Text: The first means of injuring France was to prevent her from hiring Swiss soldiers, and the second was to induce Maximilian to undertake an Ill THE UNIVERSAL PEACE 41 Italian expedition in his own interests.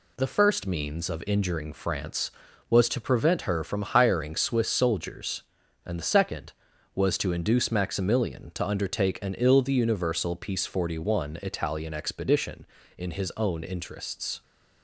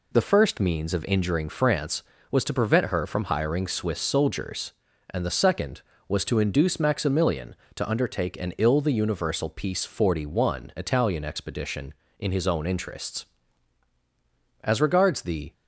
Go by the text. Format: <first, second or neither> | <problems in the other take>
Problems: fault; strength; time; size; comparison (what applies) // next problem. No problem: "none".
first | goes on to say "As regards the"; noticeable; from 14.6 s on; 0.90 s long